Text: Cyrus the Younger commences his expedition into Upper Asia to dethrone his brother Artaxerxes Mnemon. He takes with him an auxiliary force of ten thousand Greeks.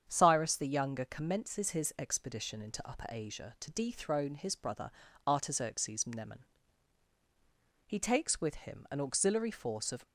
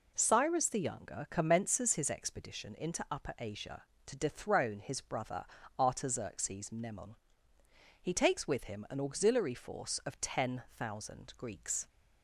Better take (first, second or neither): second